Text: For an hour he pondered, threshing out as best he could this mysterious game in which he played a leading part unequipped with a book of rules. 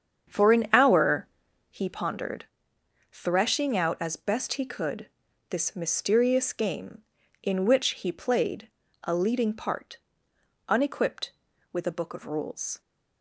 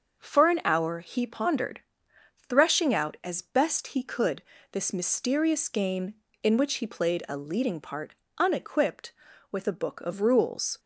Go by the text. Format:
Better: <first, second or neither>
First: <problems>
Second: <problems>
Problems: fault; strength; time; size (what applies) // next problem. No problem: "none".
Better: second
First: starts louder than the rest; strong; until 1.9 s; 7.5 dB // pauses between "hour" and "he"; at 1.2 s; 0.44 s long // pauses between "could" and "this"; at 5.0 s; 0.40 s long // pauses between "played" and "a"; slight; at 8.6 s; 0.36 s long // pauses between "part" and "unequipped"; noticeable; at 9.9 s; 0.72 s long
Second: pauses between "could" and "this"; slight; at 4.4 s; 0.28 s long // pauses between "part" and "unequipped"; slight; at 8.1 s; 0.24 s long